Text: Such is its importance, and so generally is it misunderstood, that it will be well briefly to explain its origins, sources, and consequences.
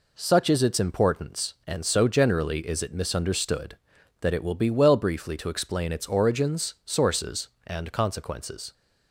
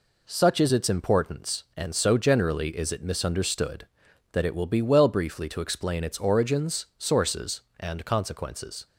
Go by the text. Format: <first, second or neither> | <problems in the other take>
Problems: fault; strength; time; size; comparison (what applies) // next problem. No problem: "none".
neither | none